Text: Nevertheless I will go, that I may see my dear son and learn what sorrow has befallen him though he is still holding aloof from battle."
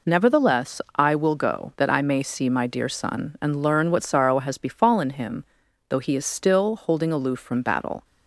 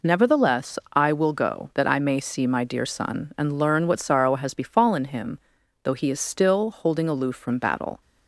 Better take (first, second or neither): neither